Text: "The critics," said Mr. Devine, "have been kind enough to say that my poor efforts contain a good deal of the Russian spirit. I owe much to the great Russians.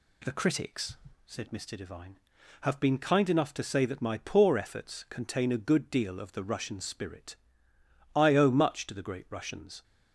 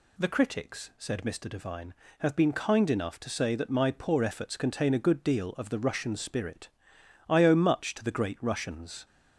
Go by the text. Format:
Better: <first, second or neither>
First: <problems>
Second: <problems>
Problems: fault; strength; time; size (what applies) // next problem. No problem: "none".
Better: neither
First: none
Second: none